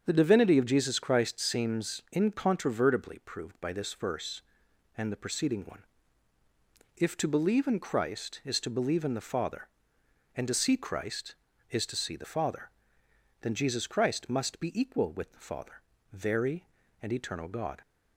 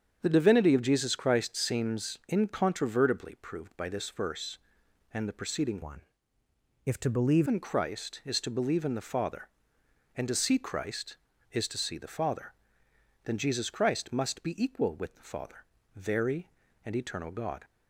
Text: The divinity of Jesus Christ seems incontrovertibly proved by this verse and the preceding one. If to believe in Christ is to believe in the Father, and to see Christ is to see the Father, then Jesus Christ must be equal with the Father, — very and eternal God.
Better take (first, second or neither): first